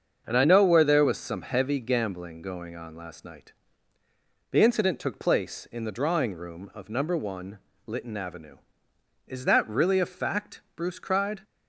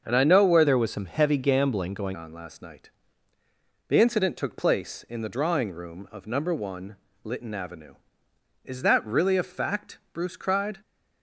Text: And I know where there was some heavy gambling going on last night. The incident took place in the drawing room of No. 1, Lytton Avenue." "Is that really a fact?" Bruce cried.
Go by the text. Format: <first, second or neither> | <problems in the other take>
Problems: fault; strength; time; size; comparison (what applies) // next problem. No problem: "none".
first | starts louder than the rest; until 1.0 s; 6.5 dB; also in the first // changes voice from "there" to "going"; from 0.6 to 2.1 s; 1.5 s long